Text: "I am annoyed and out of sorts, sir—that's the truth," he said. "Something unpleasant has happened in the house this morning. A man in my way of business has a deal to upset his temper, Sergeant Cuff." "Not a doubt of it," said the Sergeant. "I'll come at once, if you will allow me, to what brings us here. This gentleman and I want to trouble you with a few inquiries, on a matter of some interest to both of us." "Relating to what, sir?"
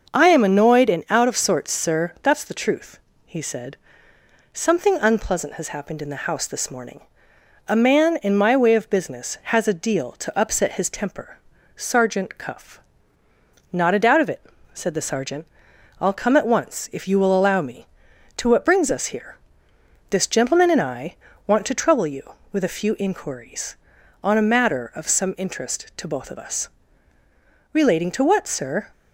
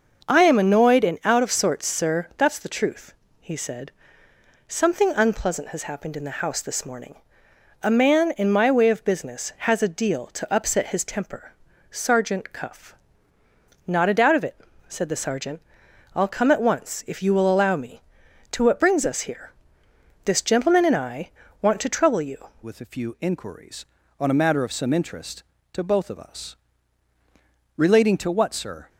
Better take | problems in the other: first | starts louder than the rest; until 1.3 s; 6.5 dB; also in the first // pauses between "I" and "want"; slight; at 21.3 s; 0.30 s long; slight in the first // changes voice at "with"; from 22.6 s on; 6.2 s long

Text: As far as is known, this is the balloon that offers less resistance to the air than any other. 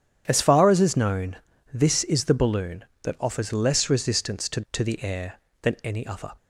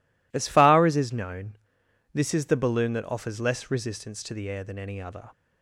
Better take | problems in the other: second | starts louder than the rest; strong; until 1.2 s; 9 dB // says "to" twice; at 4.7 s

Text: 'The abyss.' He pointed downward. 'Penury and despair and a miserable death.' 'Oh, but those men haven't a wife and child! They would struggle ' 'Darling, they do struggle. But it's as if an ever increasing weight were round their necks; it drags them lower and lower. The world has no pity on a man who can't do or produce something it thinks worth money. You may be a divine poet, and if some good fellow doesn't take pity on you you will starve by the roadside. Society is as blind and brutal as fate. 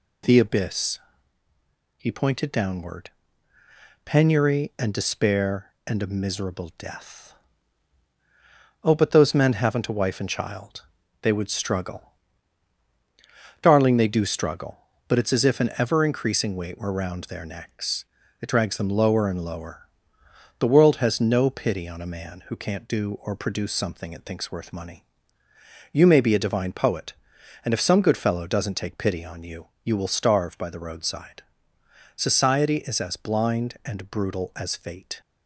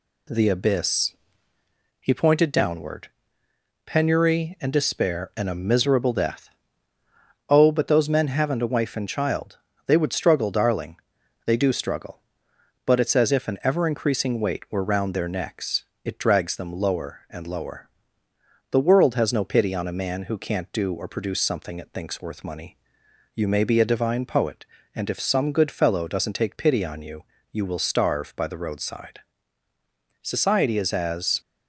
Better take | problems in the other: first | pauses between "you" and "you"; slight; at 27.2 s; 0.26 s long; slight in the first // stops before "blind and brutal as fate"; at 31.4 s

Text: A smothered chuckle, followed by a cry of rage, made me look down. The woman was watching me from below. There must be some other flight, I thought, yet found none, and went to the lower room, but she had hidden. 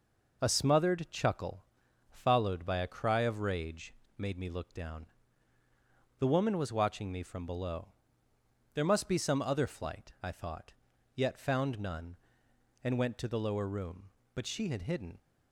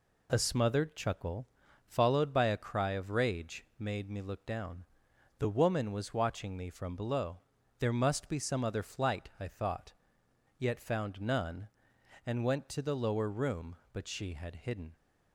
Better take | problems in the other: neither | none

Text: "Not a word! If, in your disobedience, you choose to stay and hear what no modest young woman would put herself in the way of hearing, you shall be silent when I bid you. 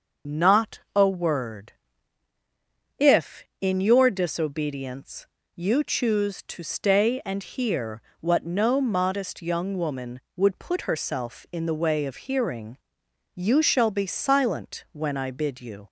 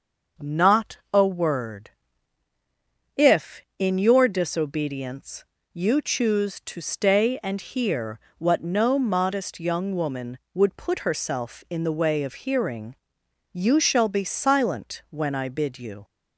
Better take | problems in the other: second | loses the start of "Not"; at 0.2 s; 45 ms // pauses between "Not" and "a"; slight; at 0.8 s; 0.16 s long; slight in the second // pauses between "hear" and "what"; slight; at 8.0 s; 0.18 s long; slight in the second

